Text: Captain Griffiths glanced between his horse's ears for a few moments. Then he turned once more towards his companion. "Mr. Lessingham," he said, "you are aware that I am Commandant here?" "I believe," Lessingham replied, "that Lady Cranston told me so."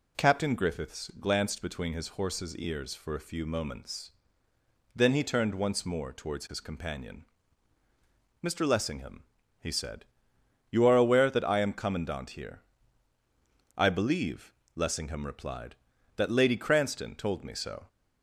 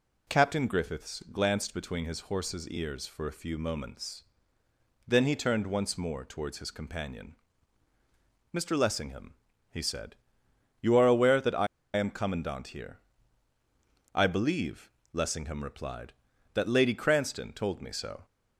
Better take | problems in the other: first | pauses between "I" and "am"; slight; at 11.6 s; 0.29 s long

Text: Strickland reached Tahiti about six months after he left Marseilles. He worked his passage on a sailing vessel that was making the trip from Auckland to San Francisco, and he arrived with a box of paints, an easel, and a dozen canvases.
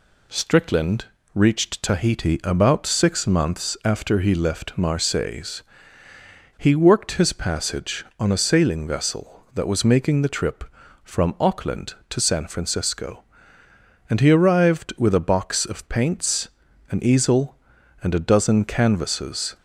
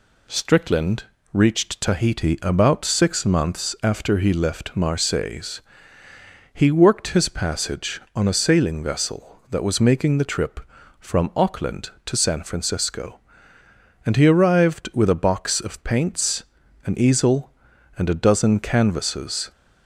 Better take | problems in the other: neither | pauses between "Strickland" and "reached"; slight; the same in both

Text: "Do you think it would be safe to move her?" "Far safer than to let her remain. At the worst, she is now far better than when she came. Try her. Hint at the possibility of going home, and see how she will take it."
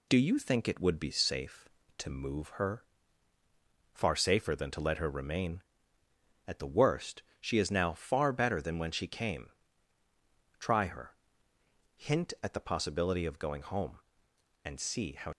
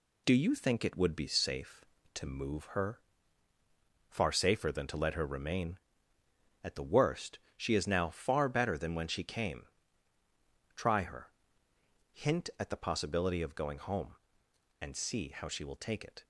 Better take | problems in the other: second | stops before "she will take it"; at 15.3 s

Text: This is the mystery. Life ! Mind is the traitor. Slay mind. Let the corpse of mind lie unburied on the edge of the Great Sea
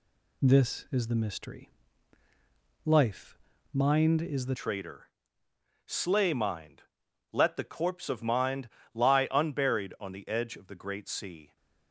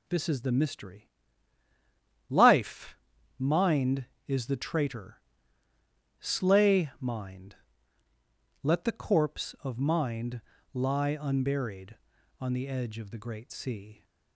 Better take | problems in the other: second | changes voice at "traitor"; from 4.5 s on; 7.0 s long // pauses between "mind" and "lie"; slight; at 8.6 s; 0.24 s long; slight in the second

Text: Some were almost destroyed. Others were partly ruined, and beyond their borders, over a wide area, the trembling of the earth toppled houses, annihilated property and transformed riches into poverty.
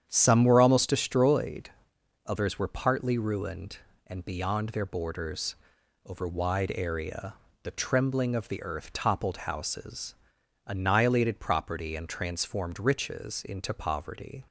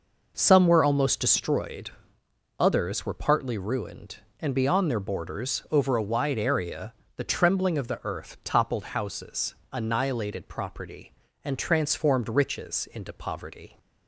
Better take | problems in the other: second | starts louder than the rest; strong; until 1.0 s; 9 dB // skips "a"; at 6.2 s

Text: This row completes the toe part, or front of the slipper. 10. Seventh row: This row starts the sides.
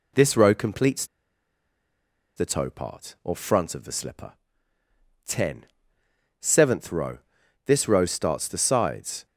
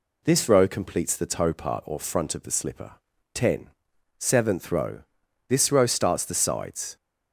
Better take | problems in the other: second | pauses between "completes" and "the"; strong; at 1.0 s; 1.3 s long

